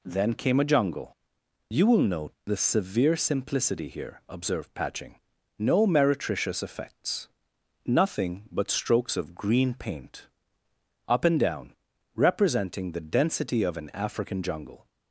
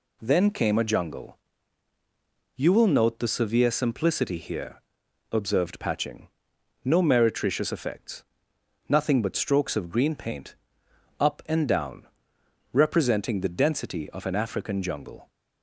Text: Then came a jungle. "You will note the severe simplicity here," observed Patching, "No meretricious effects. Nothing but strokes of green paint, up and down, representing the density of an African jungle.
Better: neither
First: none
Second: none

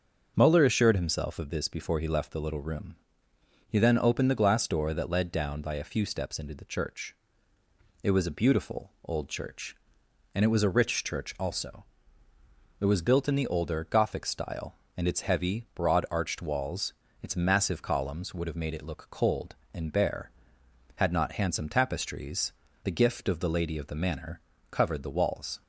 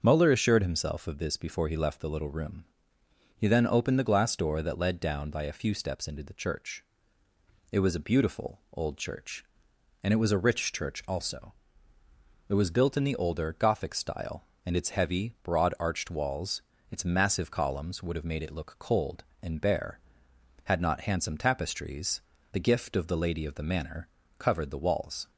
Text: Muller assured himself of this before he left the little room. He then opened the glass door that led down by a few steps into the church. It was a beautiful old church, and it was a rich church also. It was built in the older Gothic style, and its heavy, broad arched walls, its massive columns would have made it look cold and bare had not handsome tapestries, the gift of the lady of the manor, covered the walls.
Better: neither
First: starts louder than the rest; until 1.3 s; 6.5 dB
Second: starts louder than the rest; until 1.0 s; 6.5 dB

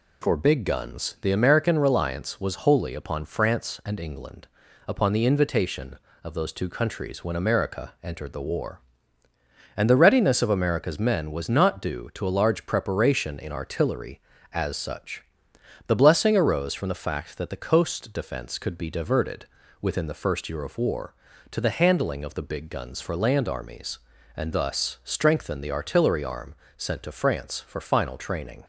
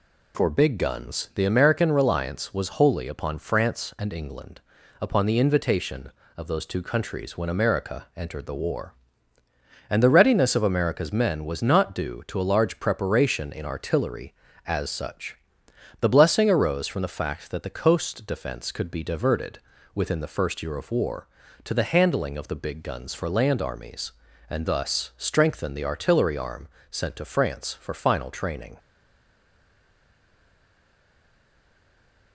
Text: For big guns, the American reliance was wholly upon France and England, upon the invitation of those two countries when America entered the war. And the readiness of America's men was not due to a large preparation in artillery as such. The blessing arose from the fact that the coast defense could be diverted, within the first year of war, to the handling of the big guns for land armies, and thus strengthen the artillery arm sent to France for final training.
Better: first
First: pauses between "arm" and "sent"; slight; at 26.5 s; 0.22 s long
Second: pauses between "arm" and "sent"; slight; at 26.6 s; 0.22 s long // stays silent after the last word; strong; from 28.7 s on; 3.6 s long

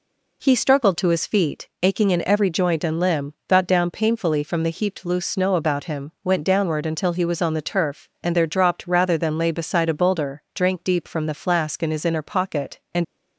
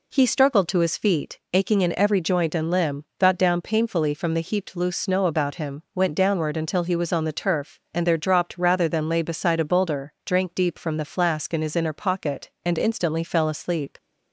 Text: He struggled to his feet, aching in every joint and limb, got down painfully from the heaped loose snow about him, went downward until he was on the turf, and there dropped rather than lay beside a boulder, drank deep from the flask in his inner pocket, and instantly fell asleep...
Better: second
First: stops before "instantly fell asleep"; at 13.0 s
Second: none

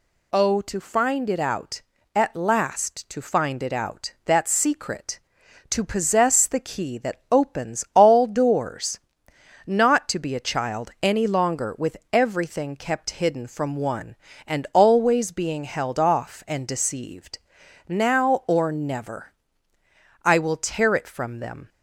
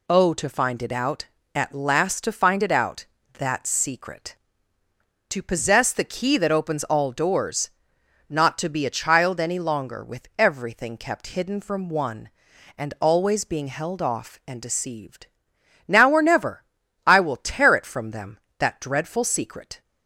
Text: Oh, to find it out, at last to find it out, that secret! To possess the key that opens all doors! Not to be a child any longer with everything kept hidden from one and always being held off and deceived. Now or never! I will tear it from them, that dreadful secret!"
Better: second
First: pauses between "with" and "everything"; slight; at 11.9 s; 0.16 s long // stops before "that dreadful secret"; at 21.6 s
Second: none

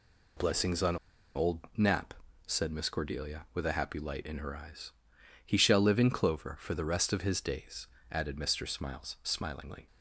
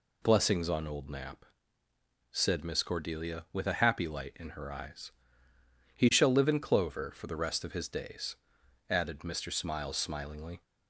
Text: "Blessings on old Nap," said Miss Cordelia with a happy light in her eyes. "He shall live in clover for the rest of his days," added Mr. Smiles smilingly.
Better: second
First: pauses between "on" and "old"; at 0.9 s; 0.39 s long // pauses between "old" and "Nap"; slight; at 1.6 s; 0.16 s long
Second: none

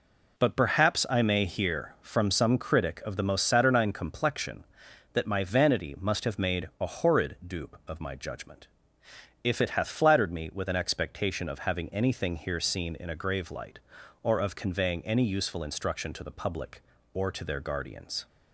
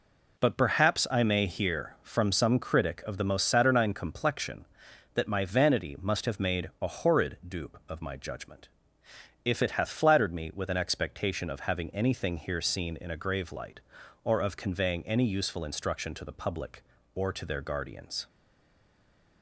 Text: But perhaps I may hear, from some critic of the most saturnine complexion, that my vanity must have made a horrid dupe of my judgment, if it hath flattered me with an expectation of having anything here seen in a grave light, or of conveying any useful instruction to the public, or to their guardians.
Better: first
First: none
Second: stays silent after the last word; from 18.2 s on; 1.2 s long

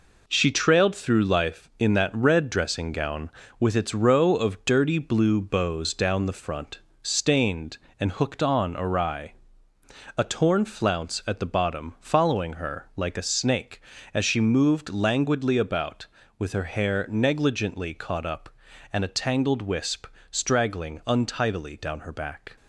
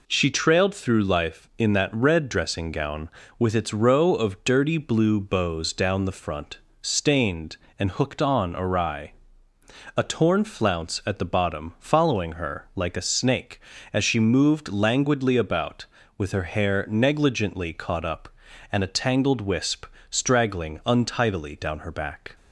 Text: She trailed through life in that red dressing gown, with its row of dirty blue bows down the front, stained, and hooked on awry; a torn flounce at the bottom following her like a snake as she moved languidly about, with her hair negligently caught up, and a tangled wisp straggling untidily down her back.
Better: second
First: gets quieter; noticeable; throughout; 5.5 dB // pauses between "wisp" and "straggling"; slight; at 20.0 s; 0.24 s long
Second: pauses between "wisp" and "straggling"; slight; at 19.8 s; 0.24 s long

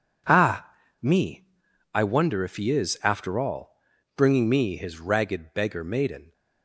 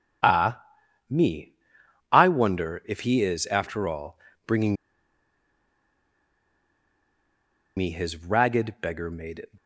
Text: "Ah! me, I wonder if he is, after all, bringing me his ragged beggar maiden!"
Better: first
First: none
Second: pauses between "bringing" and "me"; strong; at 4.7 s; 3.0 s long

